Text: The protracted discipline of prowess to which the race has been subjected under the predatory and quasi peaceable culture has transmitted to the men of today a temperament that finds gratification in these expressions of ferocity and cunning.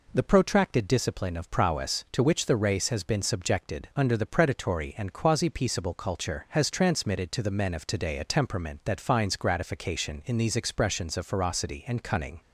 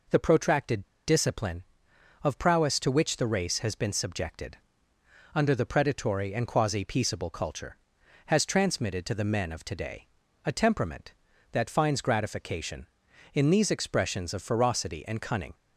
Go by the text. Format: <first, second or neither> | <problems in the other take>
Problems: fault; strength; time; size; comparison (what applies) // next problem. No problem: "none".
first | pauses between "protracted" and "discipline"; slight; at 0.8 s; 0.24 s long // pauses between "subjected" and "under"; noticeable; at 4.5 s; 0.76 s long // pauses between "today" and "a"; at 10.0 s; 0.38 s long